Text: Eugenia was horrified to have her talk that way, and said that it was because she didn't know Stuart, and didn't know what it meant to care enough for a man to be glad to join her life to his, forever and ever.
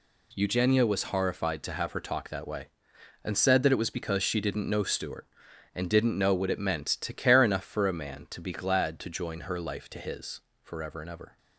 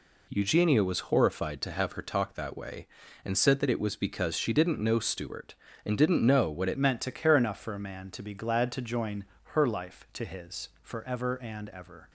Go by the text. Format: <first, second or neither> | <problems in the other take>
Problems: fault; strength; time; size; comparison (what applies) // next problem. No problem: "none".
first | changes voice at "meant"; from 6.7 s on; 5.4 s long // pauses between "join" and "her"; slight; at 9.2 s; 0.28 s long